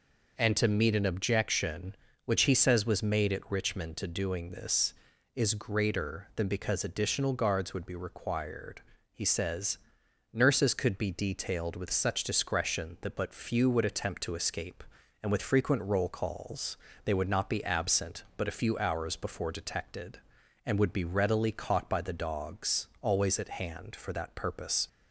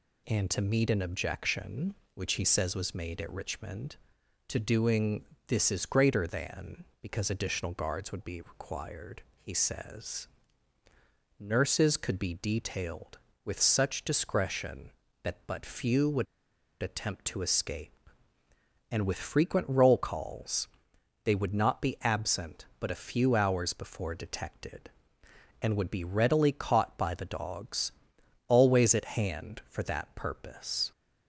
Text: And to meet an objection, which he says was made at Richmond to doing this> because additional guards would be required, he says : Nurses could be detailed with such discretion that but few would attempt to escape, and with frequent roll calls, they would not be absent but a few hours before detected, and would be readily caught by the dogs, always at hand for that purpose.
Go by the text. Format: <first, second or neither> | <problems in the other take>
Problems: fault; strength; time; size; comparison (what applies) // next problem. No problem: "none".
first | pauses between "doing" and "this"; slight; at 5.2 s; 0.24 s long // pauses between "would" and "attempt"; noticeable; at 16.2 s; 0.57 s long